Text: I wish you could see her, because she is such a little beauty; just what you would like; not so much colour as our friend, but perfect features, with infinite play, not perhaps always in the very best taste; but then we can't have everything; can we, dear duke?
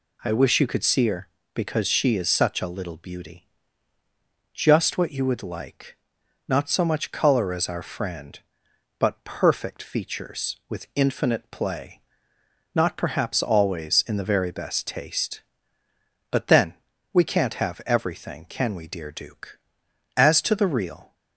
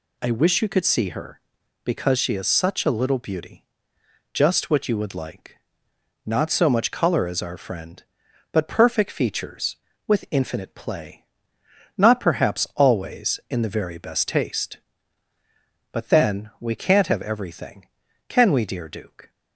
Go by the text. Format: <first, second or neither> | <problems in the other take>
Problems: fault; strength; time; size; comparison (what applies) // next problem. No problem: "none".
second | pauses between "then" and "we"; at 16.7 s; 0.40 s long // goes on to say "As to the real"; noticeable; from 20.1 s on; 0.98 s long